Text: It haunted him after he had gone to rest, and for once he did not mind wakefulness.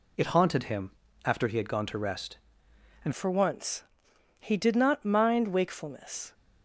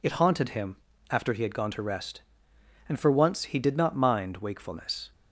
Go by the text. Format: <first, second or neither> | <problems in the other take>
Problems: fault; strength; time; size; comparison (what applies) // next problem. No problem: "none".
second | pauses between "him" and "after"; slight; at 0.9 s; 0.32 s long; slight in the second // changes voice at "for"; from 3.1 s on; 3.2 s long // pauses between "once" and "he"; noticeable; at 3.8 s; 0.56 s long